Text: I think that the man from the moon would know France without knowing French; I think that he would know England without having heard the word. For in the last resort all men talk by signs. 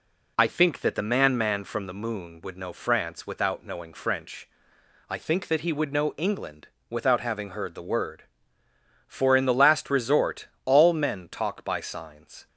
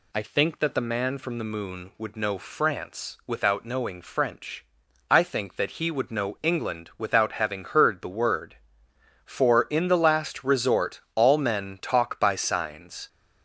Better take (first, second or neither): second